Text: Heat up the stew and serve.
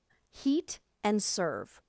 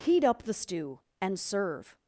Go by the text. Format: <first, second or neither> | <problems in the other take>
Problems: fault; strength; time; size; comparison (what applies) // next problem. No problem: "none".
second | skips "up the stew"; at 0.9 s